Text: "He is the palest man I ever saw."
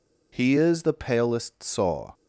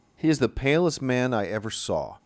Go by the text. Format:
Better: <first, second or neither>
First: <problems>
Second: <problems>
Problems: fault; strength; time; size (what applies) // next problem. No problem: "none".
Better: second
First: skips "man I ever"; at 1.6 s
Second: none